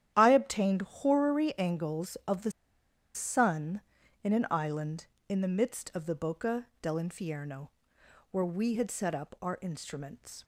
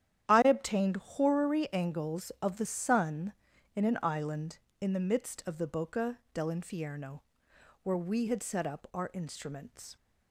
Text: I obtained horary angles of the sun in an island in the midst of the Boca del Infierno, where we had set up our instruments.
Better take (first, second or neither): second